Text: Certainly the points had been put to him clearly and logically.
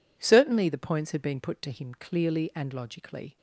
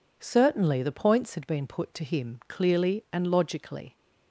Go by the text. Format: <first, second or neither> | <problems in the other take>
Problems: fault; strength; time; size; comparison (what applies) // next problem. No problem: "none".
neither | none